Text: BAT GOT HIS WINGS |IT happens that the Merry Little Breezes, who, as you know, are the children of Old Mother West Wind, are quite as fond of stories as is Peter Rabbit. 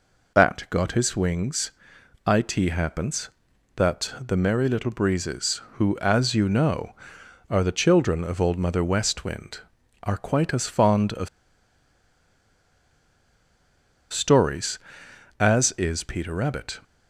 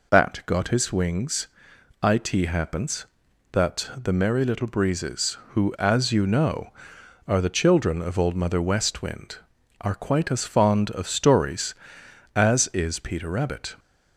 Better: second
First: pauses between "of" and "stories"; strong; at 11.2 s; 2.8 s long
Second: none

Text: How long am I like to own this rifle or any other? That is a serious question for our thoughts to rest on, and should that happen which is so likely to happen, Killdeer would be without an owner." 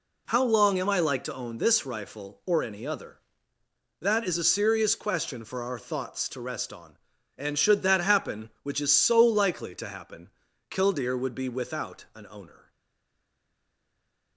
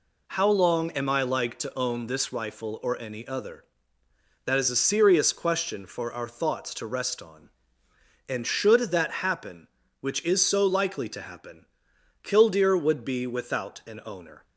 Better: second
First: stays silent after the last word; noticeable; from 12.7 s on; 1.6 s long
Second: none

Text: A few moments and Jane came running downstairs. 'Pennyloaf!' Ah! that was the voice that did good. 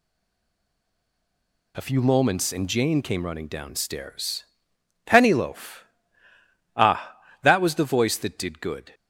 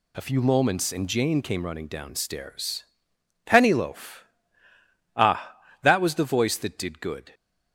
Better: second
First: stays silent before the first word; noticeable; until 1.7 s; 1.7 s long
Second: none

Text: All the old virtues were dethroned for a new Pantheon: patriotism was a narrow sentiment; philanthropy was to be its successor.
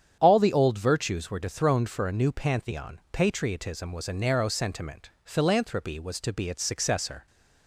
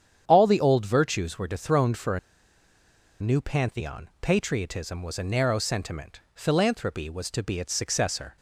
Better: first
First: starts louder than the rest; strong; until 1.2 s; 8.5 dB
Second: starts louder than the rest; strong; until 1.2 s; 8.5 dB // pauses between "a" and "new"; at 2.1 s; 1.0 s long

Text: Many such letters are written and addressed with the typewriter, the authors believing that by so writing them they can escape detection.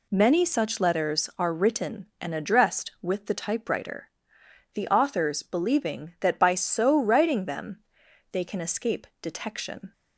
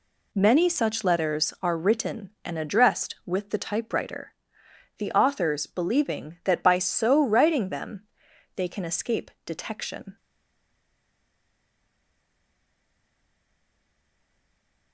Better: first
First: pauses between "them" and "they"; noticeable; at 7.7 s; 0.52 s long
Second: pauses between "them" and "they"; noticeable; at 8.0 s; 0.52 s long // stays silent after the last word; strong; from 10.1 s on; 4.8 s long

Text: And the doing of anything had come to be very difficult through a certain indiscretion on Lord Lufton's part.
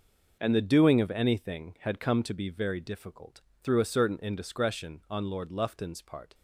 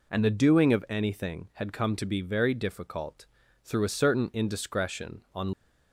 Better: first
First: pauses between "difficult" and "through"; slight; at 3.4 s; 0.24 s long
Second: pauses between "difficult" and "through"; at 3.2 s; 0.40 s long // stops before "Lord Lufton's part"; at 5.5 s

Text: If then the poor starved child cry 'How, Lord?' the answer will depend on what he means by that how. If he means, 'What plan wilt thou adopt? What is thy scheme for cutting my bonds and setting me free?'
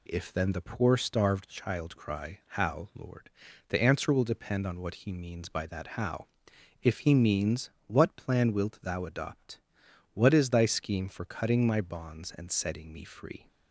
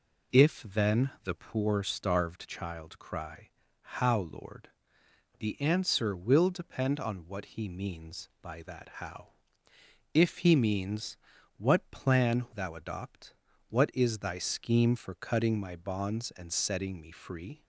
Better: first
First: none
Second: pauses between "then" and "the"; slight; at 1.0 s; 0.16 s long // pauses between "cry" and "How"; slight; at 3.4 s; 0.32 s long // skips "wilt"; at 12.4 s

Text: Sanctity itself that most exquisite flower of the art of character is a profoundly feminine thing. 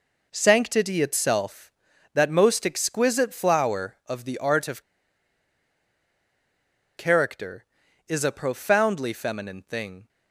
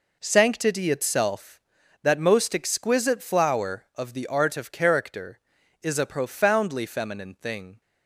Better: second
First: pauses between "of" and "character"; strong; at 4.8 s; 2.1 s long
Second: none

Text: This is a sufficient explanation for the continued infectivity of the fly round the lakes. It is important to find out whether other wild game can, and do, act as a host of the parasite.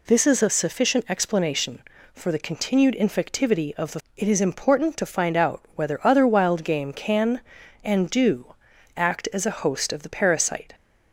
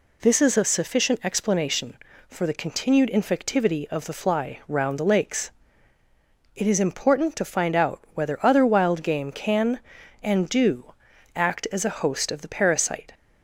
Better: second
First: skips "fly round the lakes"; at 4.0 s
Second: none

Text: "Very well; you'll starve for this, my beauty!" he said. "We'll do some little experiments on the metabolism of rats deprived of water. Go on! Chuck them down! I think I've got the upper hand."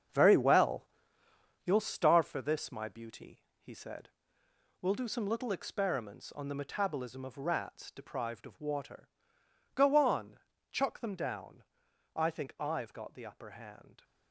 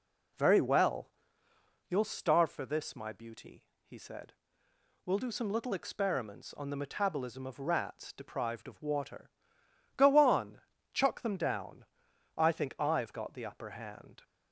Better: second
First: gets quieter; strong; throughout; 9 dB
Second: none

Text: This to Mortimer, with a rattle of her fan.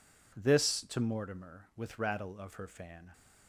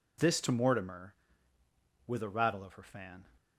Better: second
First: skips "a"; at 1.9 s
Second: none

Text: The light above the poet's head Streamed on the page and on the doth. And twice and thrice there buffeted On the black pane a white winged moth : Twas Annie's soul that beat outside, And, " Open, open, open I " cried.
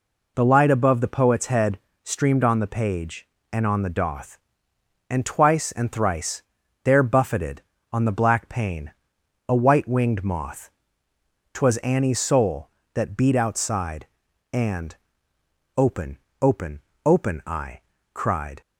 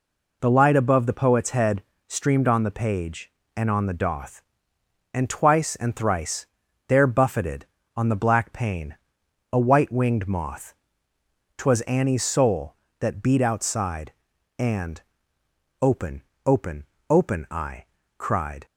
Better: neither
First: pauses between "head" and "Streamed"; slight; at 1.7 s; 0.24 s long // pauses between "thrice" and "there"; at 6.4 s; 0.42 s long // pauses between "pane" and "a"; noticeable; at 8.9 s; 0.56 s long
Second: pauses between "head" and "Streamed"; slight; at 1.8 s; 0.24 s long // pauses between "thrice" and "there"; at 6.4 s; 0.42 s long // pauses between "pane" and "a"; noticeable; at 8.9 s; 0.56 s long

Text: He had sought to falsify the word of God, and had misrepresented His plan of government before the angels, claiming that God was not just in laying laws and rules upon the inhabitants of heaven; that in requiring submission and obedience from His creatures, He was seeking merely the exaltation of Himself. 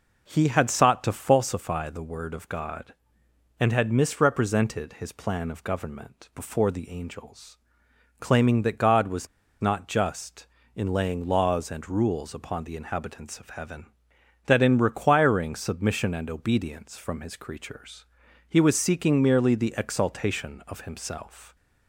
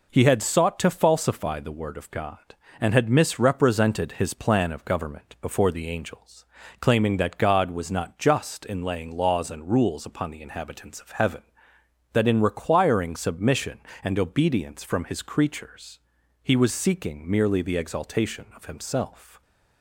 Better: second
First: pauses between "was" and "not"; slight; at 9.2 s; 0.33 s long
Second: none

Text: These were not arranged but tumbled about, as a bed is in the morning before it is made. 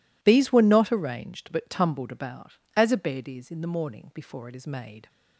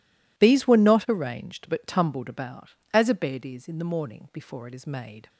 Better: neither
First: none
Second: none

